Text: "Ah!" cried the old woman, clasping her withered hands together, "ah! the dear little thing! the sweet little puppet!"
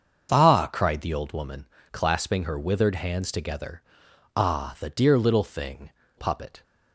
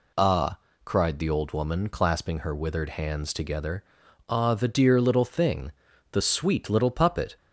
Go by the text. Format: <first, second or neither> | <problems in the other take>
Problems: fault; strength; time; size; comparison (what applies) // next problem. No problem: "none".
second | starts louder than the rest; until 1.3 s; 6.5 dB // skips "the sweet little"; at 6.0 s